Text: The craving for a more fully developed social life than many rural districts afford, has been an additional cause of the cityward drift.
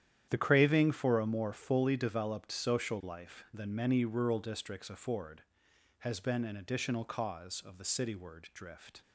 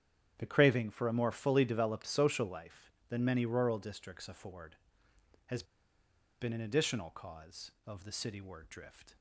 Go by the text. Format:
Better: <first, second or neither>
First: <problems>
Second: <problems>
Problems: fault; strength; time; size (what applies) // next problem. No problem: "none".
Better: first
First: starts louder than the rest; strong; until 1.3 s; 10 dB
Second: starts louder than the rest; strong; until 1.3 s; 9 dB // pauses between "has" and "been"; noticeable; at 5.6 s; 0.77 s long